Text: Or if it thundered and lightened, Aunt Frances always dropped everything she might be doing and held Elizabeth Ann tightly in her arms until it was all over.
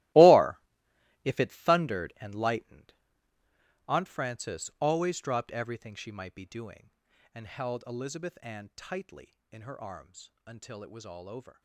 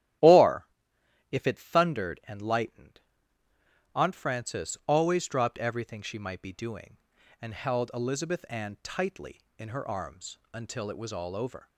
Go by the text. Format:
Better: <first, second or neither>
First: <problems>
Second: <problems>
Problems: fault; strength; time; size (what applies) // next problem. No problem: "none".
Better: second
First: gets quieter; strong; throughout; 14.5 dB // starts louder than the rest; strong; until 1.7 s; 18 dB // pauses between "Or" and "if"; noticeable; at 0.5 s; 0.64 s long // pauses between "arms" and "until"; slight; at 10.3 s; 0.16 s long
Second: starts louder than the rest; strong; until 1.8 s; 13 dB // pauses between "Or" and "if"; noticeable; at 0.6 s; 0.64 s long // pauses between "arms" and "until"; slight; at 10.3 s; 0.16 s long